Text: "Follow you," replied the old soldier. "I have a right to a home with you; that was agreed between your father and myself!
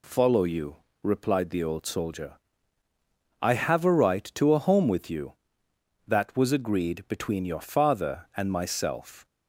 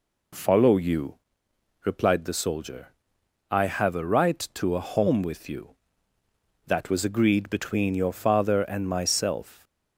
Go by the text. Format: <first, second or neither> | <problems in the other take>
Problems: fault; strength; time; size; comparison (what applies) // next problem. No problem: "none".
first | skips "old"; at 2.3 s